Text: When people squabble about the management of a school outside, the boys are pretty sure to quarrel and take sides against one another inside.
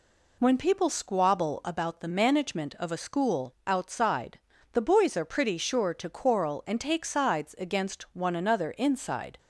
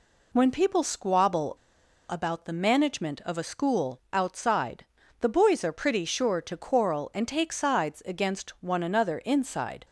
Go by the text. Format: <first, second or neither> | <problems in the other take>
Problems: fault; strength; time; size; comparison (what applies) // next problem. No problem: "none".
first | pauses between "squabble" and "about"; noticeable; at 1.5 s; 0.55 s long